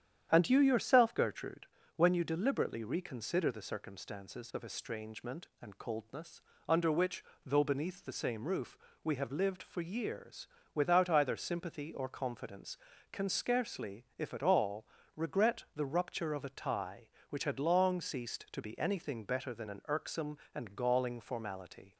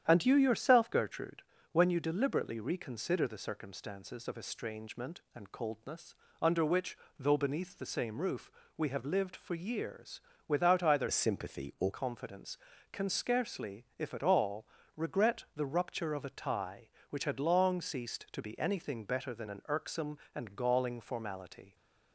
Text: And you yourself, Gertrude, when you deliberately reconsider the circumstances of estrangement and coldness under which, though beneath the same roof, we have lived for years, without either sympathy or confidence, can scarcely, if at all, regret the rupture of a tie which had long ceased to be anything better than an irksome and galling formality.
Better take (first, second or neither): first